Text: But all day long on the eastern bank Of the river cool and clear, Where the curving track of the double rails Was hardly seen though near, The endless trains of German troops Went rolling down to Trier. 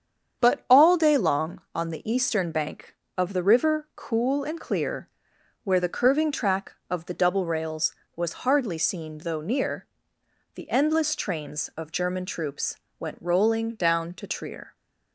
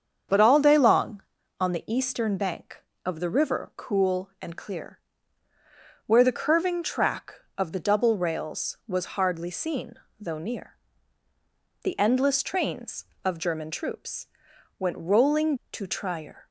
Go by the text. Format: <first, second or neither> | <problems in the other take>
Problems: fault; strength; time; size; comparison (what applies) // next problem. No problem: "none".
first | starts louder than the rest; strong; until 1.6 s; 7.5 dB; strong in the first // pauses between "seen" and "though"; slight; at 9.9 s; 0.24 s long // pauses between "troops" and "Went"; noticeable; at 14.2 s; 0.50 s long; slight in the first // skips "down"; at 15.6 s